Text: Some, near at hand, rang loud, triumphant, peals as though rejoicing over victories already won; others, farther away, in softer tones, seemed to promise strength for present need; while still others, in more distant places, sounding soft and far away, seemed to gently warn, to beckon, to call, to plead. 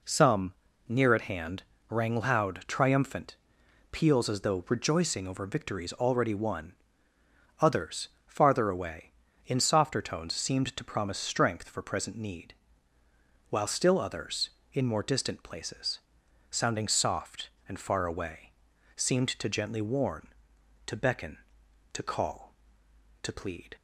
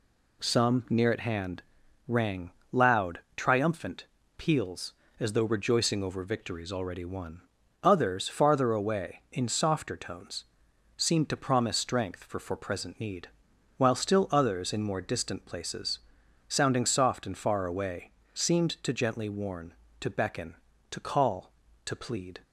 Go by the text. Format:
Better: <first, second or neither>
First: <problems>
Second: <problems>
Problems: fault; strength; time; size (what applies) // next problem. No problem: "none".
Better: first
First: none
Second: pauses between "rang" and "loud"; slight; at 2.5 s; 0.22 s long // says "for" twice; at 12.4 s